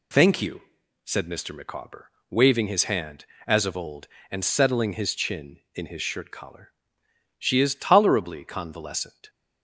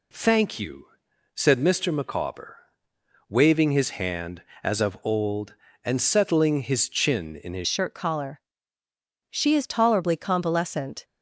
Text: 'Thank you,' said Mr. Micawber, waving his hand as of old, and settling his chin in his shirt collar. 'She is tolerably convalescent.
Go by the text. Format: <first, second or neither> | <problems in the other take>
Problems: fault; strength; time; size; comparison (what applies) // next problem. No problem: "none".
first | changes voice at "shirt"; from 7.6 s on; 3.4 s long